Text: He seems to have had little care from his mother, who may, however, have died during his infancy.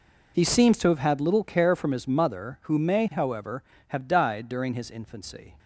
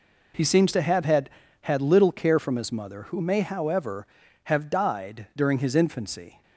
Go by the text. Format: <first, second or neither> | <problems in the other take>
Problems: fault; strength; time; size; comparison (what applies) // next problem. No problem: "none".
first | says "had" twice; at 1.6 s